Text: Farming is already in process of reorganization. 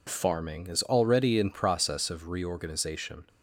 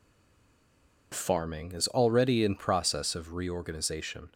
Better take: first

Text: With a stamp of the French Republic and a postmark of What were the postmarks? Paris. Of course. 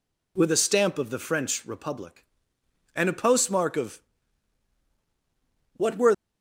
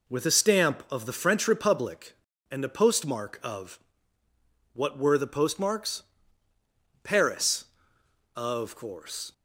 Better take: second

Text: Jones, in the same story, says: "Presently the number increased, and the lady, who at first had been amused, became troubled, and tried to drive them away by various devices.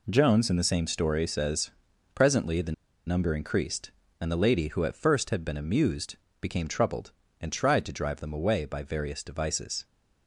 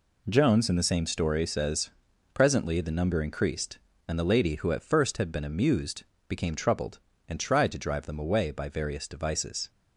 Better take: second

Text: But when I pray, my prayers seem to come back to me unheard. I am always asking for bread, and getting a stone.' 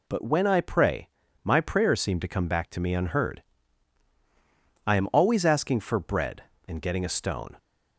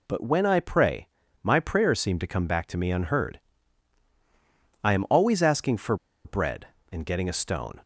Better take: first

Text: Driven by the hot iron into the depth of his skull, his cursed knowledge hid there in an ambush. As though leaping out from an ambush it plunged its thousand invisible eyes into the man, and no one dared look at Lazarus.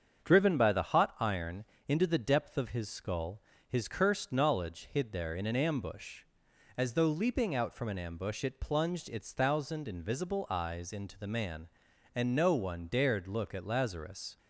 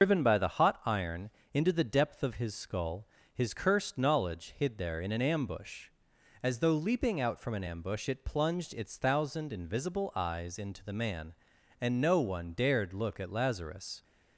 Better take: first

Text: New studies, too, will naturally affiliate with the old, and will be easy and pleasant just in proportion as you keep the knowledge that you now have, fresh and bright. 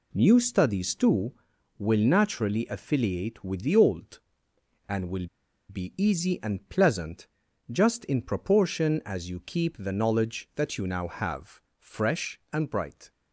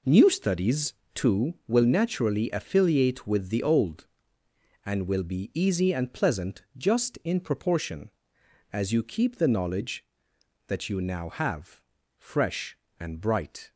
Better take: second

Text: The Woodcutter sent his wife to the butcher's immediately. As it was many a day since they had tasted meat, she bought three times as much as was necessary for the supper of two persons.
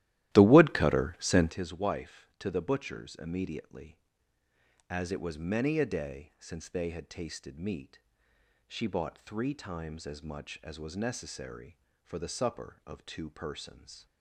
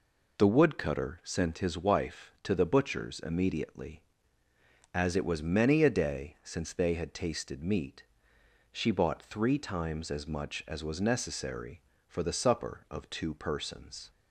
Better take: second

